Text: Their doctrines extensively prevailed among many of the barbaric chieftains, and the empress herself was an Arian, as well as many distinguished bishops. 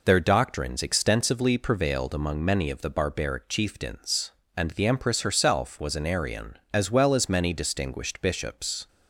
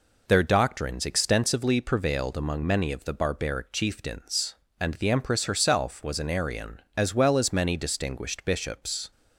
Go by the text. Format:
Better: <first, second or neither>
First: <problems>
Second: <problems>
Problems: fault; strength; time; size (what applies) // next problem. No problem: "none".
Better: neither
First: none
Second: none